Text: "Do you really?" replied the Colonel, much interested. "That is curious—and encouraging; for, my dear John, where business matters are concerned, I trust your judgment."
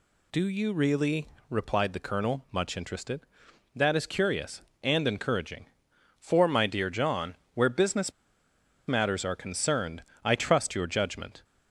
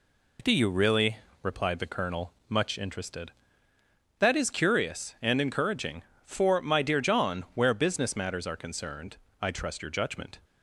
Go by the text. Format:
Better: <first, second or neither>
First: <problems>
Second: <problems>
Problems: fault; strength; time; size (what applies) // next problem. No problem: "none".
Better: second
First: pauses between "business" and "matters"; noticeable; at 8.1 s; 0.75 s long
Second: none